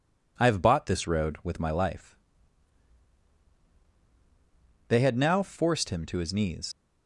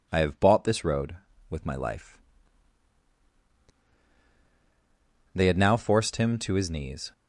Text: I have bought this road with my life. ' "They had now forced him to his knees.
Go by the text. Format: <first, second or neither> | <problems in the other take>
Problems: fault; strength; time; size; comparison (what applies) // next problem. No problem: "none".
second | leaves "knees" unfinished; at 6.7 s; 35 ms